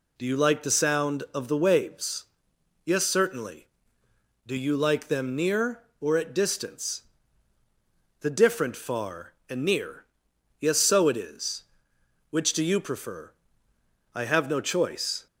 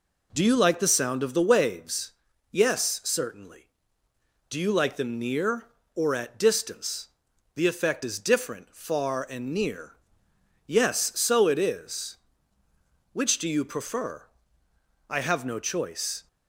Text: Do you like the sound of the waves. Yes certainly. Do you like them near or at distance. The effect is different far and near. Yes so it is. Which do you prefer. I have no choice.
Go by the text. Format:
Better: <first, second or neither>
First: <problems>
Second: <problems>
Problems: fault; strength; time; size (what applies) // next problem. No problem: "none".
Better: second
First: skips "effect is"; at 8.3 s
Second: none